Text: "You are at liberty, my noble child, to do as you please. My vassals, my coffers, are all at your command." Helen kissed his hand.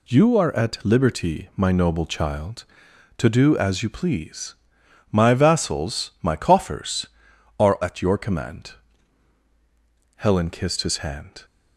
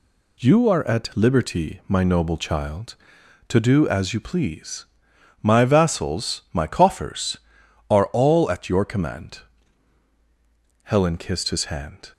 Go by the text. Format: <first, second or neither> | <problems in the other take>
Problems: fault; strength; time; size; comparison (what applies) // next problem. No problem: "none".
second | skips "all"; at 7.7 s